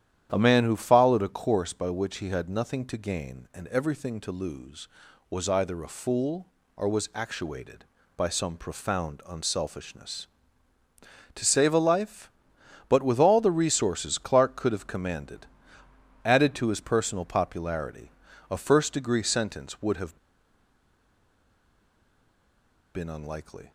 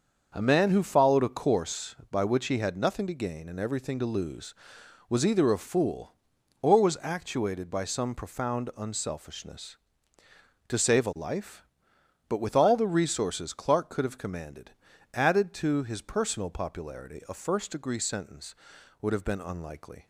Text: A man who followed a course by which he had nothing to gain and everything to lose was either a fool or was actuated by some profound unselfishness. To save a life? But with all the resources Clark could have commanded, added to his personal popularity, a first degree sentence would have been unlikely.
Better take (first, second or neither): second